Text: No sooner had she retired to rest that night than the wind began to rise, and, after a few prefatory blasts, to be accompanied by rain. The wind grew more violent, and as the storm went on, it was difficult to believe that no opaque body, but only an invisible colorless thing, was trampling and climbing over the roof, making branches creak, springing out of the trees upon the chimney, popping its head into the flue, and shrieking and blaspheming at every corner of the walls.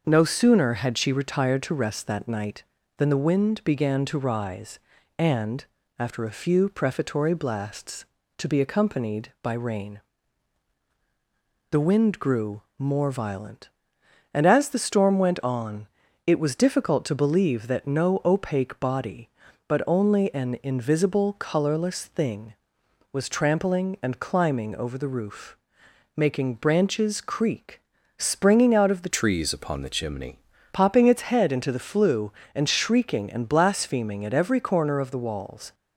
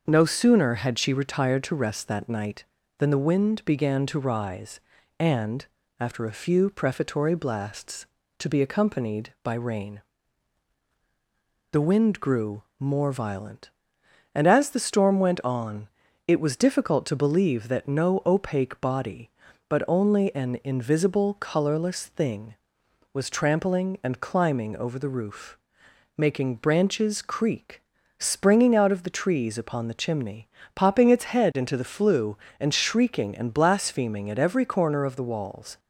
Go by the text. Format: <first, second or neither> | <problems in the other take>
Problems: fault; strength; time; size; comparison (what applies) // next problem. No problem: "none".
second | starts louder than the rest; until 1.0 s; 6.5 dB; also in the second // pauses between "grew" and "more"; slight; at 12.6 s; 0.16 s long; slight in the second // changes voice from "trees" to "chimney"; from 29.1 to 30.3 s; 1.2 s long